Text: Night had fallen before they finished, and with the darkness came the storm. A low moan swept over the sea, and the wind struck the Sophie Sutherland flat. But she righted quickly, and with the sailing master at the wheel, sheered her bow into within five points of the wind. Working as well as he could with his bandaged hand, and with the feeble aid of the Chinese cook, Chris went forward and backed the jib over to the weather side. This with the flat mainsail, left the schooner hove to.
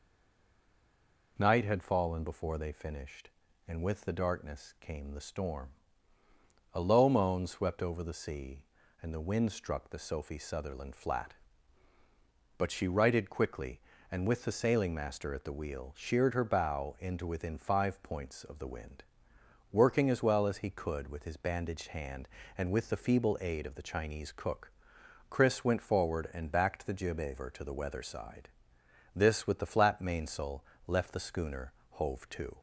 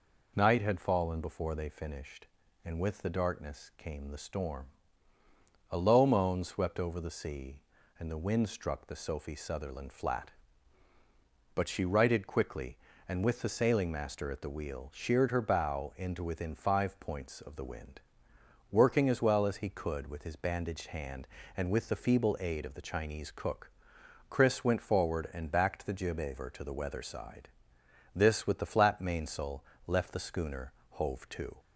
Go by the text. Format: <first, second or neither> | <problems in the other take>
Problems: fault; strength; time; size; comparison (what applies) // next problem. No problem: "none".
second | stays silent before the first word; noticeable; until 1.3 s; 1.3 s long // pauses between "schooner" and "hove"; slight; at 31.7 s; 0.20 s long; slight in the second